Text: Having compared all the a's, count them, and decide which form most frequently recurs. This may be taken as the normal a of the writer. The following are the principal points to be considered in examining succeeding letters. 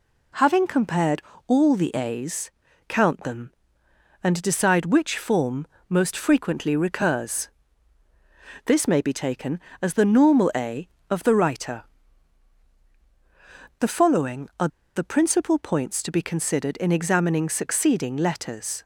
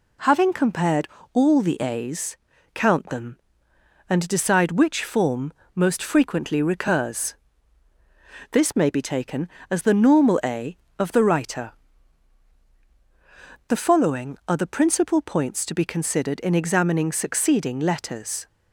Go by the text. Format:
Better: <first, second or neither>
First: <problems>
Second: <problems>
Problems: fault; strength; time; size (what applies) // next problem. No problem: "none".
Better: second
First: pauses between "compared" and "all"; slight; at 1.2 s; 0.24 s long // pauses between "form" and "most"; slight; at 5.6 s; 0.20 s long // pauses between "are" and "the"; slight; at 14.6 s; 0.28 s long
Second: pauses between "compared" and "all"; slight; at 1.0 s; 0.24 s long // pauses between "form" and "most"; slight; at 5.5 s; 0.20 s long